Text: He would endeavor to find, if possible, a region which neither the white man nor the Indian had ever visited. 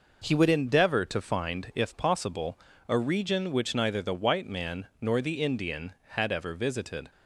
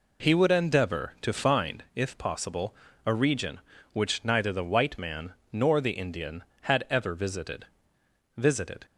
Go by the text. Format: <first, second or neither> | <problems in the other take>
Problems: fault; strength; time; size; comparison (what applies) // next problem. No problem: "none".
first | pauses between "man" and "nor"; slight; at 5.3 s; 0.18 s long // says "visited" twice; at 8.3 s